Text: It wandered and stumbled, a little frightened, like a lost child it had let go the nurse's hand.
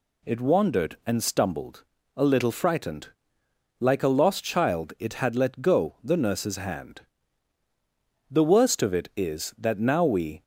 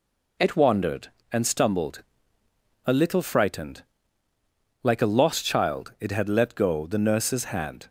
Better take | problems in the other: second | goes on to say "The worst of it is that now we"; strong; from 8.2 s on; 2.1 s long

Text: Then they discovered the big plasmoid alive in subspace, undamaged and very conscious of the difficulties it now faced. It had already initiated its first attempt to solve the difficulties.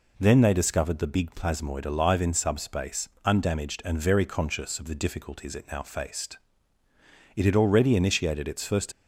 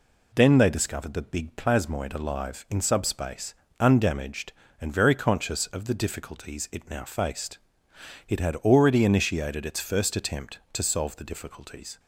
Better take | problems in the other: second | stops before "attempt to solve the difficulties"; at 8.9 s

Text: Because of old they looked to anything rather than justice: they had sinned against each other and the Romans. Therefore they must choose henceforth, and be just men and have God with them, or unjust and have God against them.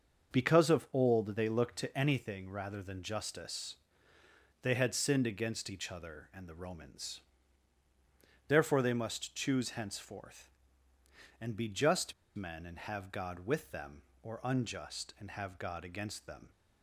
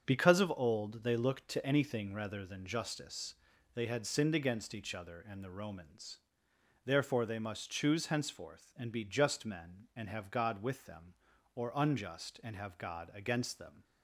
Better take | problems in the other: second | starts louder than the rest; until 1.4 s; 6.5 dB; strong in the second // pauses between "just" and "men"; slight; at 12.1 s; 0.22 s long

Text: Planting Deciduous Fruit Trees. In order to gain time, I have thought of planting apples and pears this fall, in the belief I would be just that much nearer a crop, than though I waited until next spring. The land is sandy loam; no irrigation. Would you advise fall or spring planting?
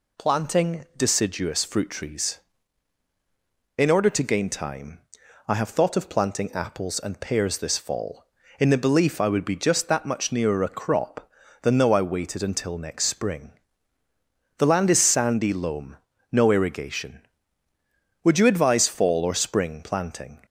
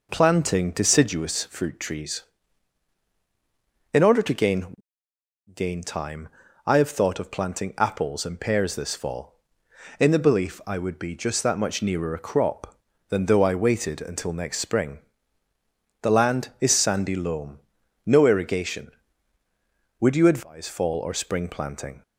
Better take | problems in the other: first | says "gain" twice; at 5.5 s

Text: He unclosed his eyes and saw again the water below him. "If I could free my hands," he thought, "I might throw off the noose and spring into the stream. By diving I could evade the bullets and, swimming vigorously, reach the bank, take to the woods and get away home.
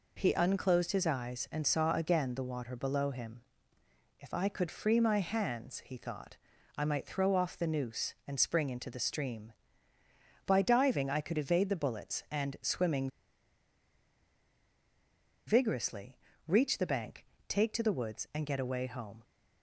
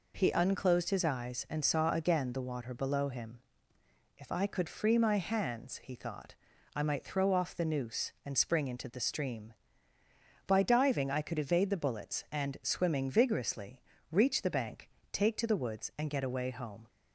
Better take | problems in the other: second | pauses between "swimming" and "vigorously"; strong; at 13.0 s; 2.3 s long

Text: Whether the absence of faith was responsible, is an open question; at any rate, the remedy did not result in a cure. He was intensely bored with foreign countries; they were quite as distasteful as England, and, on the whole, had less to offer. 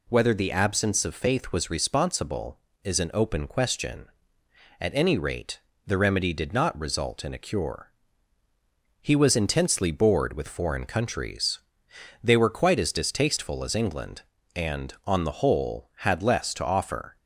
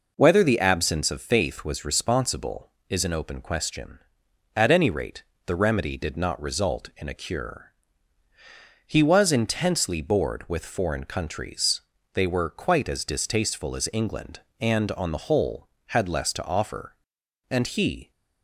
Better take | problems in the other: first | goes on to say "And he"; noticeable; from 17.4 s on; 0.62 s long

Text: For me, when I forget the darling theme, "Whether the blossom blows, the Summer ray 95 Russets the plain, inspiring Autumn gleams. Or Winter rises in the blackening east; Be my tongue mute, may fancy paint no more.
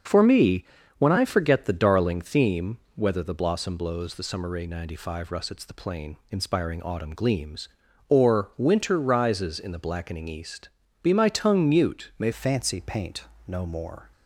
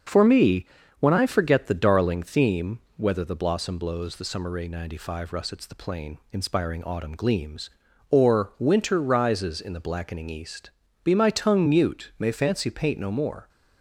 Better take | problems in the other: second | starts louder than the rest; until 1.4 s; 6.5 dB; also in the second // changes voice at "fancy"; from 12.3 s on; 1.8 s long // pauses between "paint" and "no"; slight; at 13.2 s; 0.24 s long

